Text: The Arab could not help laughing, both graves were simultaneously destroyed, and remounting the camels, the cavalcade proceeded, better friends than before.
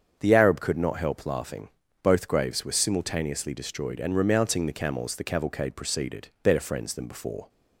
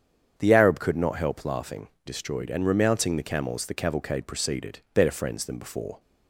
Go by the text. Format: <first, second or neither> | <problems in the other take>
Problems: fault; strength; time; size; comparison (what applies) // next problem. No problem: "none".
first | starts louder than the rest; strong; until 1.3 s; 8 dB; strong in the first // skips "both graves were simultaneously"; at 1.9 s